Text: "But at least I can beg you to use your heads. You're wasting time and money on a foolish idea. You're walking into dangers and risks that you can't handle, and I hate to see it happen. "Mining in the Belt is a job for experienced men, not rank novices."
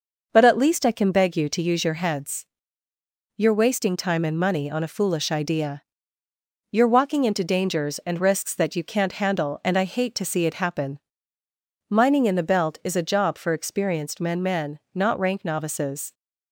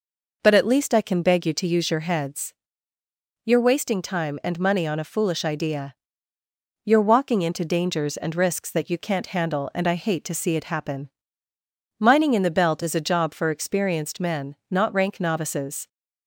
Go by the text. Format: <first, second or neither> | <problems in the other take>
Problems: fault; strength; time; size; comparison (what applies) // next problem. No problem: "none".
second | says "men" twice; at 14.4 s